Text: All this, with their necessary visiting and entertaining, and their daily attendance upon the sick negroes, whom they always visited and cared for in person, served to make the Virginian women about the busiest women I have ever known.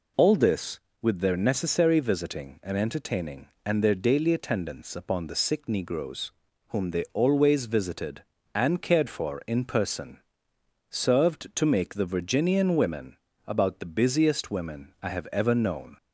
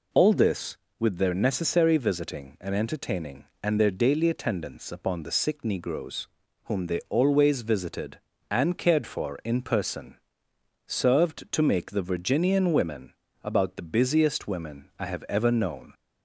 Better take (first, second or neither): neither